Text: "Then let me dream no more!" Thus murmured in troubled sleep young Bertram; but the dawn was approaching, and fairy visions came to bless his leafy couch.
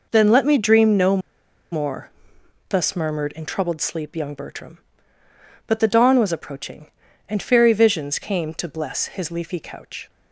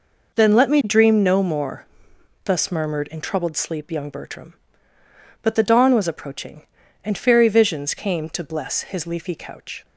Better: second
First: pauses between "no" and "more"; noticeable; at 1.1 s; 0.53 s long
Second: none

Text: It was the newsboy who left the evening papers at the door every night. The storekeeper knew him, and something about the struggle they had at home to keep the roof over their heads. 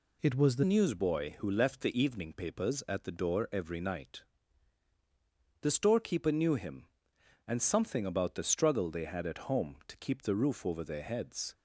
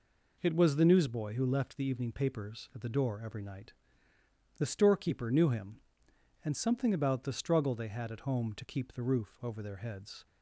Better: second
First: changes voice at "newsboy"; from 0.6 s on; 10.9 s long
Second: none

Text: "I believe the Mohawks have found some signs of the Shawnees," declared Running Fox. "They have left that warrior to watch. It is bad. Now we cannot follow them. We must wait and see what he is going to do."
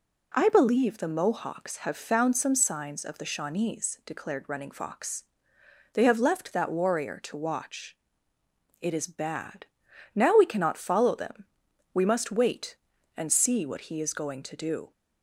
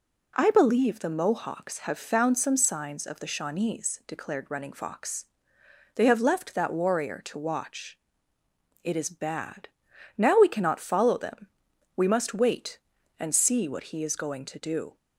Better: neither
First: none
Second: none

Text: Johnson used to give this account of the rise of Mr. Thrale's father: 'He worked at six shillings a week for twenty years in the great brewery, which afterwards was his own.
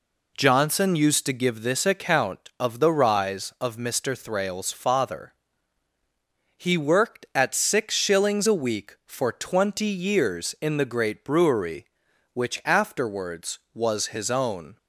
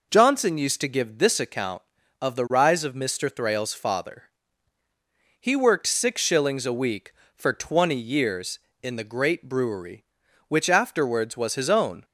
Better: first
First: none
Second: skips "at"; at 5.8 s

